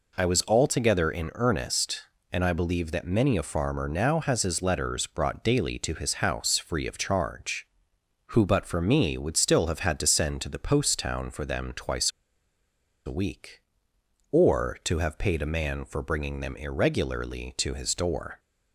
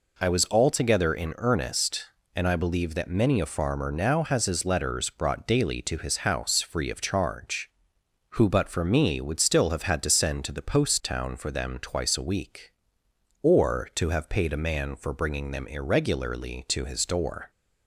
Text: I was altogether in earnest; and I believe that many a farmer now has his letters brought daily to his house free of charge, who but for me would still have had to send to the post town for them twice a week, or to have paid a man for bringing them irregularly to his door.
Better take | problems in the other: second | pauses between "twice" and "a"; noticeable; at 12.1 s; 0.96 s long

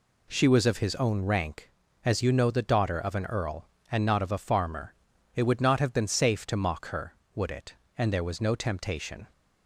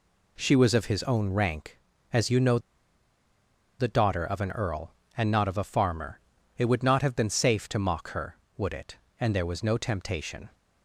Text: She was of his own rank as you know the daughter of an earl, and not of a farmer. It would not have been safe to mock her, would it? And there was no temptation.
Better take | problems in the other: first | pauses between "know" and "the"; at 2.5 s; 1.2 s long

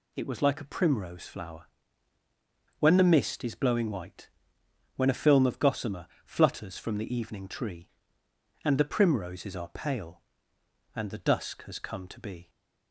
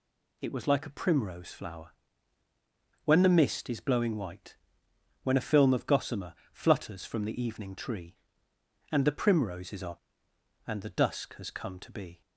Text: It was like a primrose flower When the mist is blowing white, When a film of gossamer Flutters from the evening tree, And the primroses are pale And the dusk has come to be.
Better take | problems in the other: first | pauses between "flower" and "When"; at 1.9 s; 1.1 s long; also in the first // pauses between "gossamer" and "Flutters"; slight; at 6.3 s; 0.18 s long; slight in the first // skips "pale"; at 10.3 s

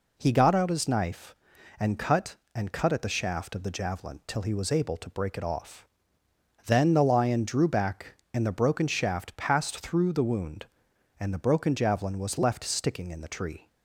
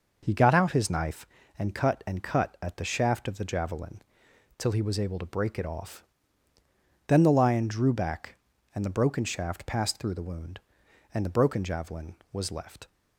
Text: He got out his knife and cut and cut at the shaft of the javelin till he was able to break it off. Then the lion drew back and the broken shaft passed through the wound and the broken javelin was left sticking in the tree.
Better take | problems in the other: first | pauses between "javelin" and "till"; noticeable; at 3.9 s; 0.58 s long // stops before "sticking in the tree"; at 12.8 s

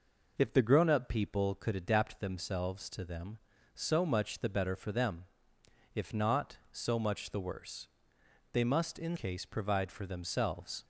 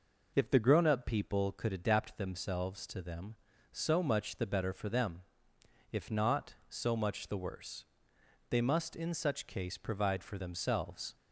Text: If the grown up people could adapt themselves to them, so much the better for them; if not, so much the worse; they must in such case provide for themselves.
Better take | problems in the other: second | skips "such"; at 9.1 s

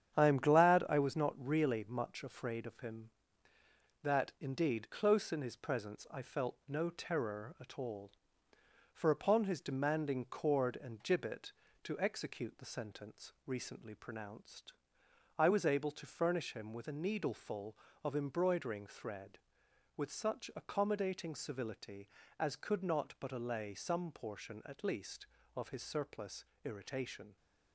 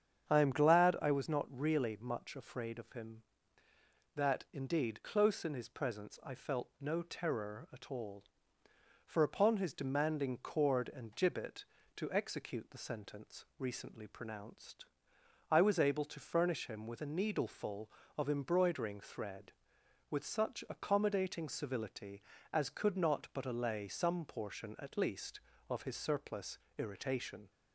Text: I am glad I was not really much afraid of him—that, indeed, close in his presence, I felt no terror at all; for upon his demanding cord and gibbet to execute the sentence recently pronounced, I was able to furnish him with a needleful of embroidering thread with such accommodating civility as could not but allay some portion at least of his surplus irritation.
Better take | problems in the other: second | gets quieter; throughout; 6.5 dB // starts louder than the rest; strong; until 1.1 s; 9 dB; strong in the second // pauses between "surplus" and "irritation"; slight; at 26.4 s; 0.22 s long; slight in the second

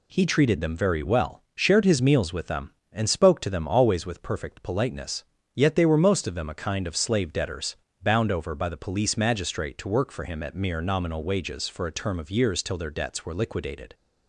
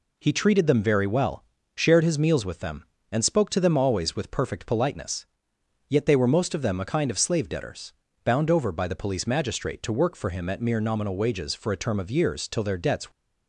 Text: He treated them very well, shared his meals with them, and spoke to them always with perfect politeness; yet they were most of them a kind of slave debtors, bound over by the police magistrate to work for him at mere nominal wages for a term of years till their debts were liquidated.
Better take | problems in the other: first | stops before "were liquidated"; at 13.1 s

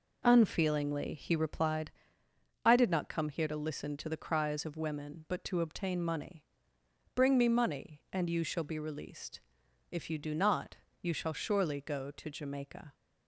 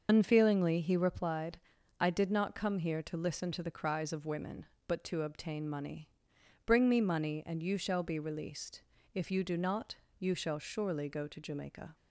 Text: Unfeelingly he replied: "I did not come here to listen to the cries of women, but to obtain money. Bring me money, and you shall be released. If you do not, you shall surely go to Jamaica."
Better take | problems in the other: first | loses the start of "Unfeelingly"; at 0.0 s; 60 ms // starts louder than the rest; noticeable; until 1.1 s; 6 dB

